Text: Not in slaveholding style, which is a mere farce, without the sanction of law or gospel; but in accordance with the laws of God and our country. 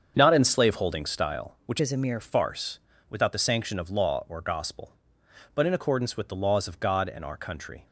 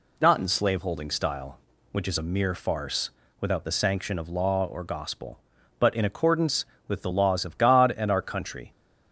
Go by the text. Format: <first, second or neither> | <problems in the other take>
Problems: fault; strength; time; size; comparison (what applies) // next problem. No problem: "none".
second | starts louder than the rest; strong; until 1.1 s; 7.5 dB // changes voice from "is" to "mere"; from 1.7 to 2.1 s; 0.4 s long